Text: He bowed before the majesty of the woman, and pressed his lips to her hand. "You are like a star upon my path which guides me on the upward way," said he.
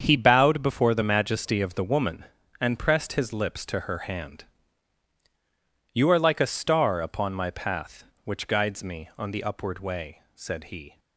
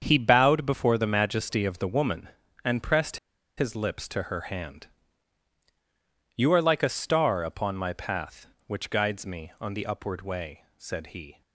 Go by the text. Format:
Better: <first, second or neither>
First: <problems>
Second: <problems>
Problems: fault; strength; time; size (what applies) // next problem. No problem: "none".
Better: first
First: starts louder than the rest; strong; until 1.0 s; 7 dB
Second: starts louder than the rest; strong; until 1.0 s; 7 dB // pauses between "pressed" and "his"; at 3.1 s; 0.40 s long